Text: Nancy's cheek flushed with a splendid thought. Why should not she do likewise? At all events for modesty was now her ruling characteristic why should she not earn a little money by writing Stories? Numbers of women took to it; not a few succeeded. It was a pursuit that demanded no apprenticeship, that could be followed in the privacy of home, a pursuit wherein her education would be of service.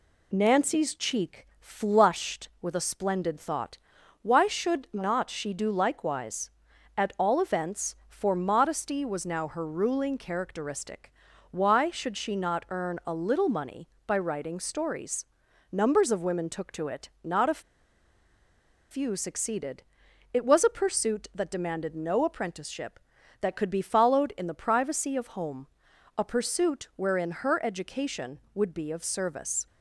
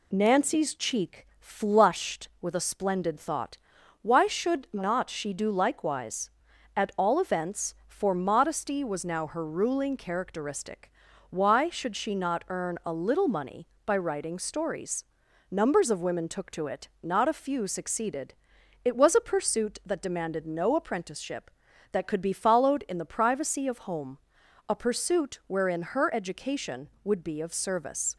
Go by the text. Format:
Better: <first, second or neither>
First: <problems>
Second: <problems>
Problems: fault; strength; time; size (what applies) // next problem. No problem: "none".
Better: second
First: pauses between "characteristic" and "why"; at 11.1 s; 0.38 s long // pauses between "a" and "few"; strong; at 17.5 s; 1.3 s long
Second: pauses between "characteristic" and "why"; at 10.9 s; 0.38 s long